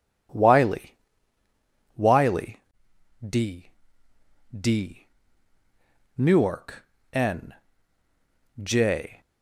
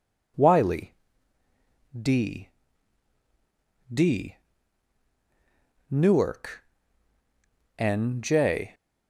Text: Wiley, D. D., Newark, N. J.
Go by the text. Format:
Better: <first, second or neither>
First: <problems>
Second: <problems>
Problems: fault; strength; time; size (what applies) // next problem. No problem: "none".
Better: second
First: says "Wiley" twice; at 1.9 s // pauses between "N" and "J"; at 7.5 s; 1.1 s long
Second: none